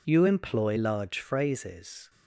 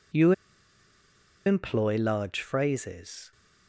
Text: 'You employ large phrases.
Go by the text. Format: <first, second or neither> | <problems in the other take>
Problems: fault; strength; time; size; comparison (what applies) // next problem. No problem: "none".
first | pauses between "You" and "employ"; at 0.3 s; 1.1 s long